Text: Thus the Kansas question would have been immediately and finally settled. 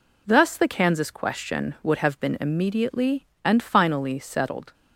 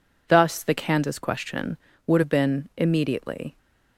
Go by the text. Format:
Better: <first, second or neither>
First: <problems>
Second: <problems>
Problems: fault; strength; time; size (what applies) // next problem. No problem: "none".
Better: first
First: none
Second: stops before "and finally settled"; at 3.5 s